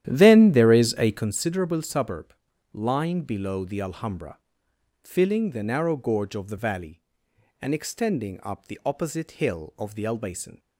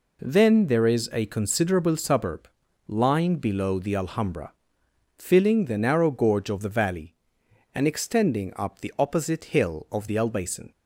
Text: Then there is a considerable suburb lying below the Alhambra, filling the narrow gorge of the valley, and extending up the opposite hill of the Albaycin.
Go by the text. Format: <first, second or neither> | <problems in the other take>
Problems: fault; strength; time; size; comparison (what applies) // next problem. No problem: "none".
second | starts louder than the rest; strong; until 1.4 s; 11.5 dB // pauses between "suburb" and "lying"; at 2.3 s; 0.40 s long; also in the second